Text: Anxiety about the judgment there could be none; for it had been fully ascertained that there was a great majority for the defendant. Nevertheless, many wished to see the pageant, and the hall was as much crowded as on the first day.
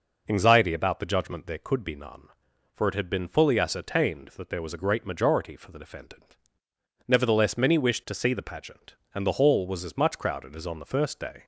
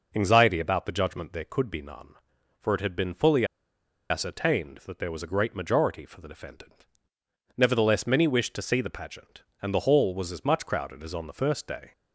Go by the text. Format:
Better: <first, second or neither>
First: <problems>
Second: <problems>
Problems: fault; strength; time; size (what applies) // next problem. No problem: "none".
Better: first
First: none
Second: pauses between "fully" and "ascertained"; noticeable; at 3.4 s; 0.65 s long